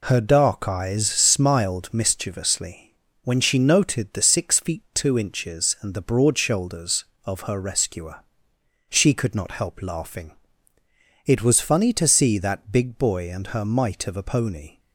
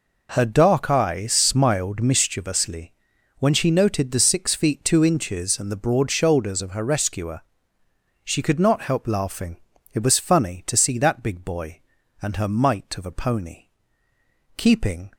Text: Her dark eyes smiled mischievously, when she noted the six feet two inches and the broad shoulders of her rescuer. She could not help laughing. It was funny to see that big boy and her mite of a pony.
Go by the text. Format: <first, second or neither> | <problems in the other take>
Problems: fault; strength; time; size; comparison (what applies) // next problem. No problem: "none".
first | goes on to say "Keeping"; from 14.5 s on; 0.54 s long